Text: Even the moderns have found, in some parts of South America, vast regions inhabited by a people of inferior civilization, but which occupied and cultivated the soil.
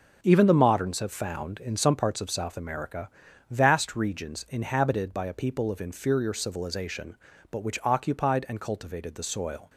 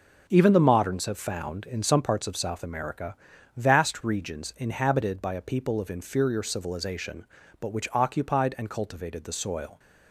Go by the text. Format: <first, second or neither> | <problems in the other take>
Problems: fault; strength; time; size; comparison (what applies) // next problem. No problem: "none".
neither | none